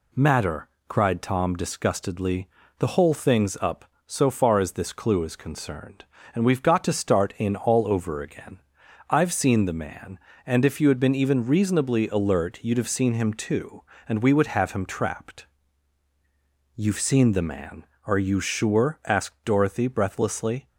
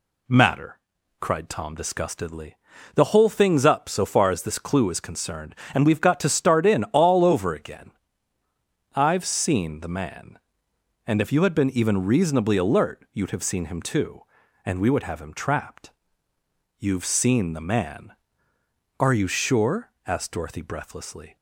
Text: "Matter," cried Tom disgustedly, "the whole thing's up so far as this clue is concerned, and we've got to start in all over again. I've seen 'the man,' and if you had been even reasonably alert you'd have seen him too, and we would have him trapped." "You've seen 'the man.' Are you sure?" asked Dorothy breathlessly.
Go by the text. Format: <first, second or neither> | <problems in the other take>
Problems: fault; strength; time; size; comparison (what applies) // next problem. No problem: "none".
neither | none